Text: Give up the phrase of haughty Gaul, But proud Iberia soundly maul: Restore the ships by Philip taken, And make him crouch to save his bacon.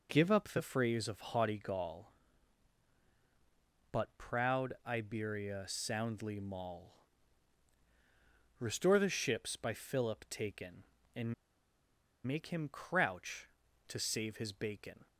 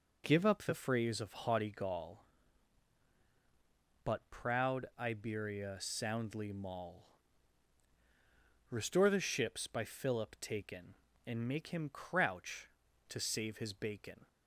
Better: second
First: pauses between "And" and "make"; noticeable; at 11.3 s; 0.92 s long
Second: none

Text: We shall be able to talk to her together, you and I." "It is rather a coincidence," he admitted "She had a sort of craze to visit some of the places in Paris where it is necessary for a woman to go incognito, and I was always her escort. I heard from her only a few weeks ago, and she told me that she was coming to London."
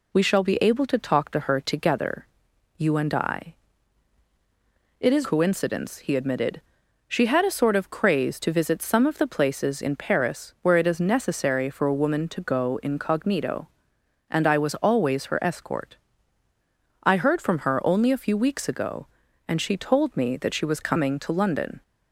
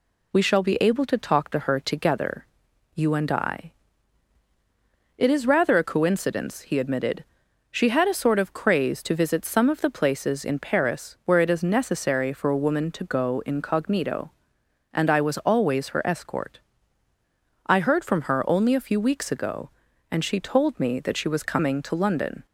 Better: second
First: skips "rather a"; at 5.2 s // pauses between "admitted" and "She"; noticeable; at 6.6 s; 0.46 s long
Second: pauses between "admitted" and "She"; noticeable; at 7.2 s; 0.46 s long

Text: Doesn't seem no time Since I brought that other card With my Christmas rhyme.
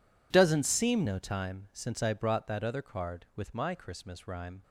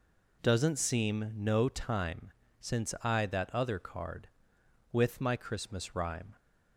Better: first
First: none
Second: pauses between "time" and "Since"; slight; at 2.3 s; 0.30 s long // skips "brought"; at 3.2 s

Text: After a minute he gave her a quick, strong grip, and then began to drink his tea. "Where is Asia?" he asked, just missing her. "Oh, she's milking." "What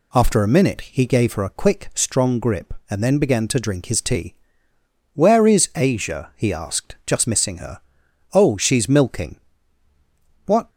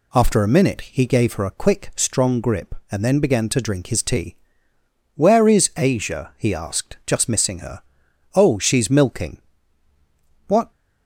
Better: neither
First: none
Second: none

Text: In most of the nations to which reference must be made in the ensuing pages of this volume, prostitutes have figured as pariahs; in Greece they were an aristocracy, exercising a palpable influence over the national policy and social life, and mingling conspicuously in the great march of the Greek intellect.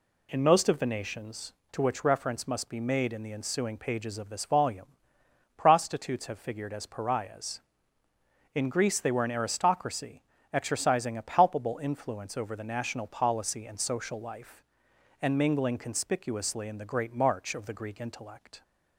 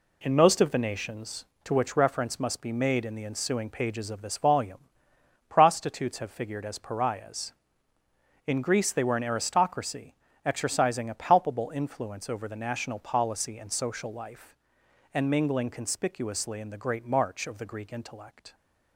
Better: first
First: none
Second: gets quieter; throughout; 7 dB

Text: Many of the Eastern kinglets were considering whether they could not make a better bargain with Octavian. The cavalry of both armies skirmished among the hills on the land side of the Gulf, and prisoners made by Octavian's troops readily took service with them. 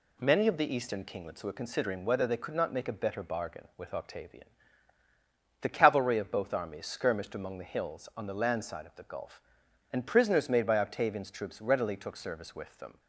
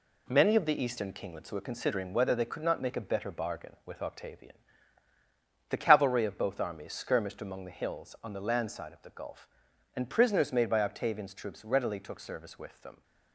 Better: first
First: none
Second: gets quieter; noticeable; throughout; 6 dB

